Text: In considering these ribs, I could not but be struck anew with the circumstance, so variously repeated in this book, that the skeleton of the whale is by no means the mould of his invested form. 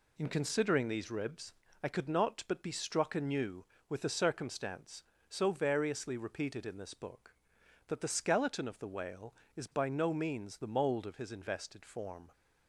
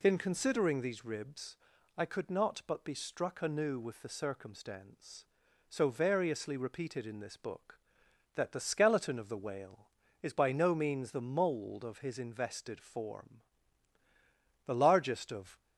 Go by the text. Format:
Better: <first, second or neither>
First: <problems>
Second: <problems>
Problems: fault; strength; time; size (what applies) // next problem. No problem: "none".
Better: first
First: none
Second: goes on to say "The largest of"; noticeable; from 14.6 s on; 0.94 s long